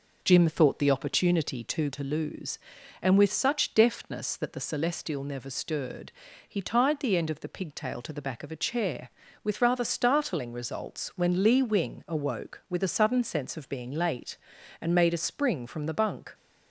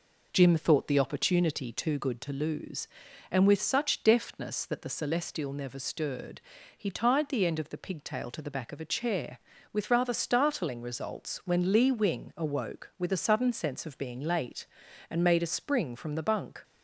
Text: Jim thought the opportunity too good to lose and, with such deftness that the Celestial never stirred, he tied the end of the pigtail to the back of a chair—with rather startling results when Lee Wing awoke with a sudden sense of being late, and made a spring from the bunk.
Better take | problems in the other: second | skips "good"; at 1.9 s

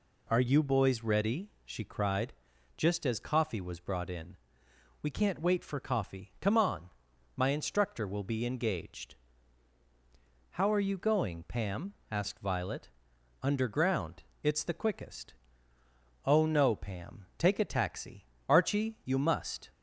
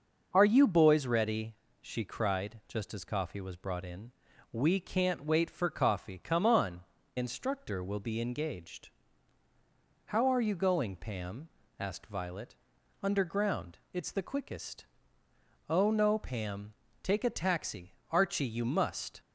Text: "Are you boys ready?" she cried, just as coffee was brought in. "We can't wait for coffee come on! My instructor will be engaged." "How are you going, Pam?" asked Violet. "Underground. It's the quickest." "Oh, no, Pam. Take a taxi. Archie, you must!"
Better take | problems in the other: first | starts louder than the rest; until 1.3 s; 6 dB // skips "My"; at 7.0 s

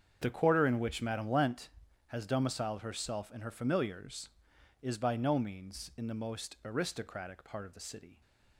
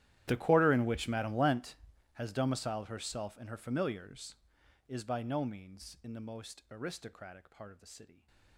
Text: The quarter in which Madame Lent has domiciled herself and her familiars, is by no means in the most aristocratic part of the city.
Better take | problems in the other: first | gets quieter; strong; throughout; 23 dB // starts louder than the rest; strong; until 1.2 s; 12.5 dB; strong in the first

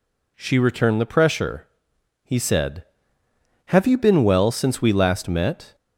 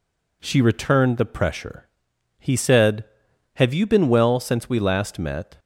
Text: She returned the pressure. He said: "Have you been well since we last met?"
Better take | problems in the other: neither | none

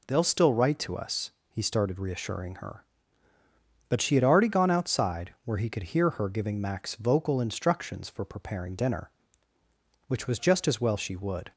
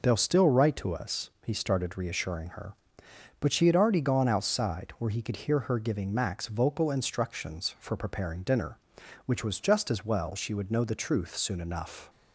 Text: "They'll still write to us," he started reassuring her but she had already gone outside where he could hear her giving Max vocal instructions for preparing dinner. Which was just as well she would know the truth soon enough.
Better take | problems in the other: second | stops before "know the truth soon enough"; at 11.5 s

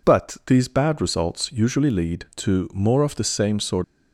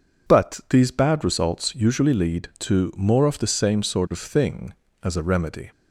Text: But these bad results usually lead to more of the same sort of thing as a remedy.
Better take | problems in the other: second | stops before "of thing as a remedy"; at 3.8 s

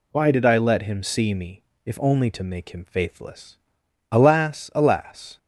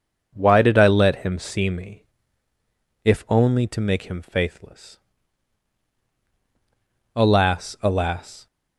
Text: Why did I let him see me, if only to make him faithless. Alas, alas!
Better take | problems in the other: neither | none

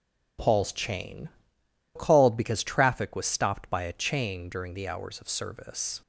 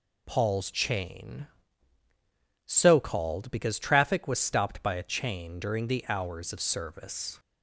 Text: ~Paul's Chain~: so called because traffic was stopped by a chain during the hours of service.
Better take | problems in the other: second | skips "so"; at 1.6 s

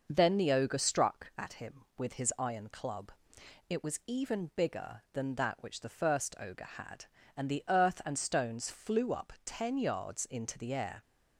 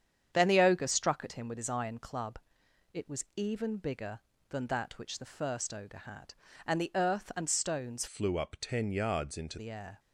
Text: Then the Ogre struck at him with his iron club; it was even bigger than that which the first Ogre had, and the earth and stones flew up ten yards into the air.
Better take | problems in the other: first | starts louder than the rest; strong; until 1.3 s; 8.5 dB // changes voice from "flew" to "into"; from 8.0 to 9.5 s; 1.5 s long

